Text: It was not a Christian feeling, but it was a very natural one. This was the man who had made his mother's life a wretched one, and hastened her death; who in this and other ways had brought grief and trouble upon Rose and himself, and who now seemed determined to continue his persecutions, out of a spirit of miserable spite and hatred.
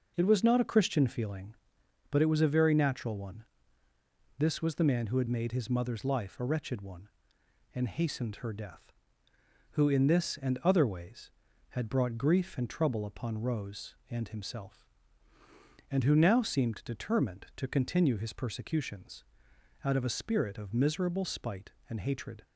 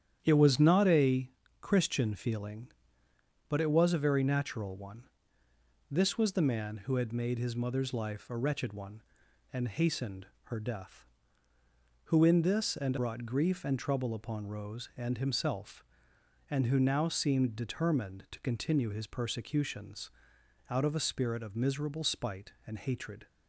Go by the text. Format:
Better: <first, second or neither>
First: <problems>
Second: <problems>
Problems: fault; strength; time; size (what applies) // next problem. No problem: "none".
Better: first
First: none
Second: starts louder than the rest; strong; until 1.2 s; 9.5 dB // pauses between "a" and "Christian"; slight; at 1.3 s; 0.32 s long // pauses between "hastened" and "her"; slight; at 10.2 s; 0.18 s long // skips "other ways had"; at 12.9 s